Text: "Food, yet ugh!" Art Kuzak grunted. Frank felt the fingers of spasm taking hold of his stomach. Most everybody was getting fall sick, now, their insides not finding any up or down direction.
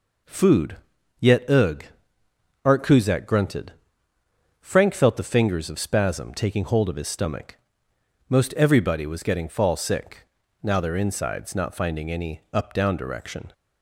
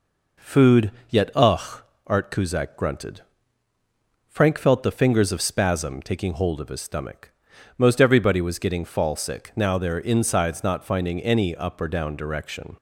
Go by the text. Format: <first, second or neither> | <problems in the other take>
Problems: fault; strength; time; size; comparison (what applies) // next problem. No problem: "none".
second | skips "or"; at 12.7 s